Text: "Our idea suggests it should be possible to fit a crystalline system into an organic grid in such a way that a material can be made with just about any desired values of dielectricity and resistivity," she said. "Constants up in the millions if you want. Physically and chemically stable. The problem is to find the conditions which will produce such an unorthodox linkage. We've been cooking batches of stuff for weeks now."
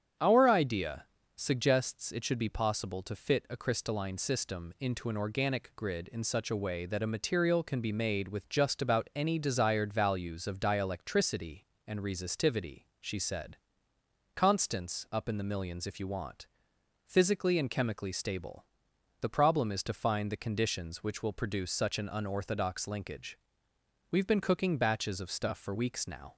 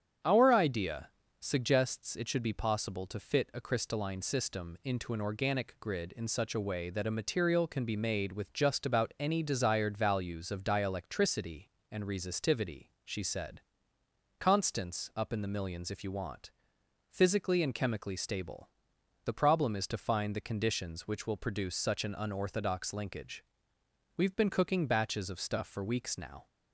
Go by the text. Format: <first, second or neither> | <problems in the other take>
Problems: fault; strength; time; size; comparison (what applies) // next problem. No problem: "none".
neither | starts louder than the rest; strong; the same in both // pauses between "idea" and "suggests"; slight; the same in both